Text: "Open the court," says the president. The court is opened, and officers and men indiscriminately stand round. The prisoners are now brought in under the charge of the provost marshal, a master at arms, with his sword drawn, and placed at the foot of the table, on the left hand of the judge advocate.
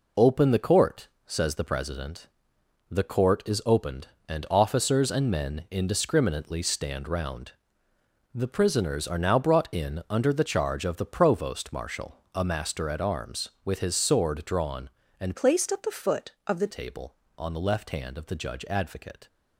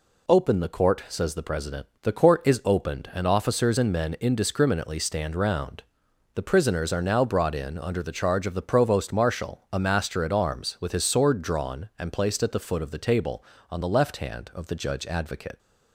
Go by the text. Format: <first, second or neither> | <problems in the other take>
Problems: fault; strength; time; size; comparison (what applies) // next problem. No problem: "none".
second | changes voice from "placed" to "the"; from 15.3 to 16.6 s; 1.3 s long